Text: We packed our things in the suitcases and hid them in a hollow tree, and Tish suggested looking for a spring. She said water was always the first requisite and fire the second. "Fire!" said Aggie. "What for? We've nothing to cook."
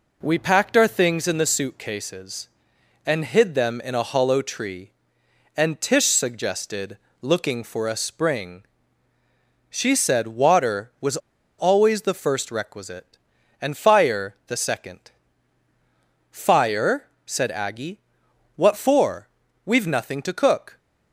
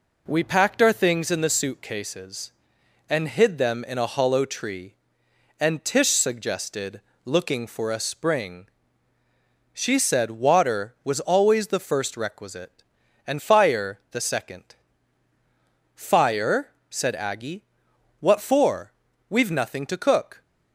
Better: second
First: pauses between "suggested" and "looking"; slight; at 6.9 s; 0.24 s long // pauses between "was" and "always"; at 11.1 s; 0.42 s long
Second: pauses between "suggested" and "looking"; slight; at 7.0 s; 0.24 s long

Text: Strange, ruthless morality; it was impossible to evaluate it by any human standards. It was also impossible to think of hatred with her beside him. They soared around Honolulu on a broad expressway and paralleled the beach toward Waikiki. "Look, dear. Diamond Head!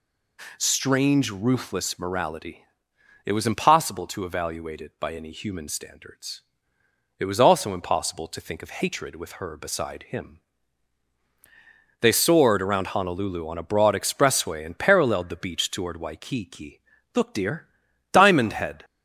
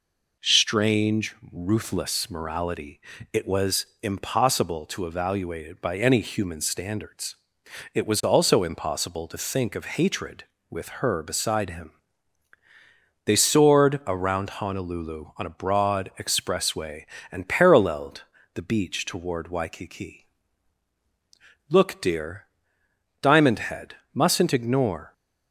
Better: first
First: none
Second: pauses between "was" and "impossible"; slight; at 3.8 s; 0.18 s long // pauses between "paralleled" and "the"; slight; at 18.2 s; 0.32 s long // goes on to say "Mustn't ignore"; noticeable; from 24.1 s on; 0.98 s long

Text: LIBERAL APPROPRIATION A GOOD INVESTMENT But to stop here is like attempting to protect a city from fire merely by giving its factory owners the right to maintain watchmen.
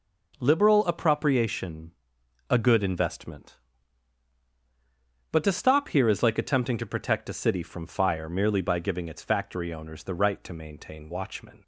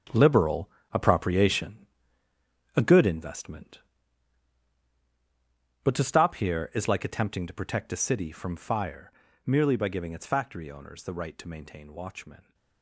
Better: first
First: pauses between "APPROPRIATION" and "A"; noticeable; at 1.9 s; 0.58 s long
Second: gets quieter; strong; throughout; 13 dB // pauses between "LIBERAL" and "APPROPRIATION"; slight; at 0.6 s; 0.24 s long // pauses between "APPROPRIATION" and "A"; noticeable; at 1.7 s; 0.98 s long // pauses between "fire" and "merely"; slight; at 9.1 s; 0.32 s long

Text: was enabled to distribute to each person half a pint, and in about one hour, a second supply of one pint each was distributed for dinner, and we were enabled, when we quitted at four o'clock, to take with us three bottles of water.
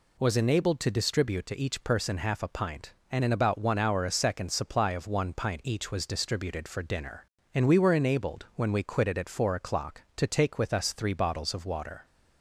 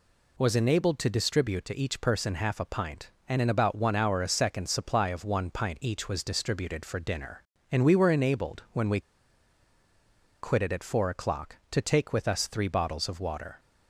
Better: first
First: none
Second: pauses between "we" and "quitted"; strong; at 9.0 s; 1.4 s long

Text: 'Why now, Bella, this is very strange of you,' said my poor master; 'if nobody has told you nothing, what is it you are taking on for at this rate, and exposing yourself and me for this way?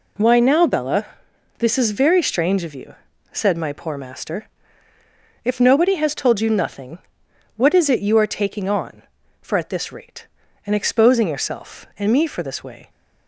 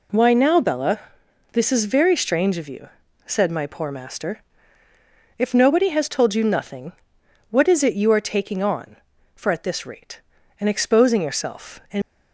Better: first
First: none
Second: stops before "me for this way"; at 12.0 s

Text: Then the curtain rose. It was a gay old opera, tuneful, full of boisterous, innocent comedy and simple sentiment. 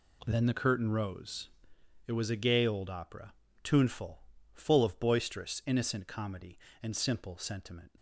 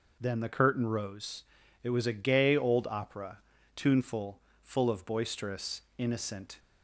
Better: first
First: none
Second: stops before "comedy and simple sentiment"; at 6.5 s

